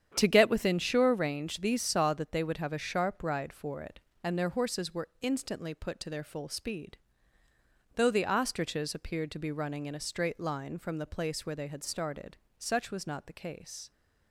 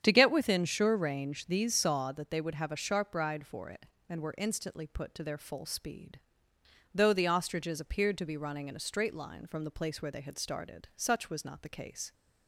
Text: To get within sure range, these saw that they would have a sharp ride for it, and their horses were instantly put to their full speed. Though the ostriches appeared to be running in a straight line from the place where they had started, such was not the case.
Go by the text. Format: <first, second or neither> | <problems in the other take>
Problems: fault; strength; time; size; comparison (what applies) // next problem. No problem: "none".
first | starts louder than the rest; strong; until 1.0 s; 8.5 dB; strong in the first // skips "their horses"; at 4.2 s